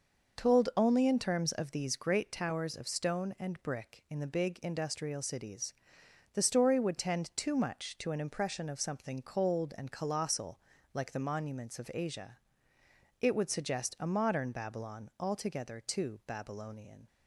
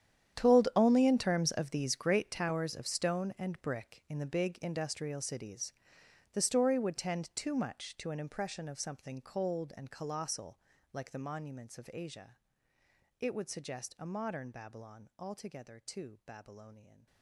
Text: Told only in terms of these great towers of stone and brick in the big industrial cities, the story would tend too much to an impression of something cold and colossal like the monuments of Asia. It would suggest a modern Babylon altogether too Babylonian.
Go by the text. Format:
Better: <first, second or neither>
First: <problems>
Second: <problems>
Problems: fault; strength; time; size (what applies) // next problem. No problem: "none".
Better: first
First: pauses between "colossal" and "like"; slight; at 10.5 s; 0.34 s long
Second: gets quieter; strong; throughout; 17.5 dB // pauses between "colossal" and "like"; slight; at 10.5 s; 0.34 s long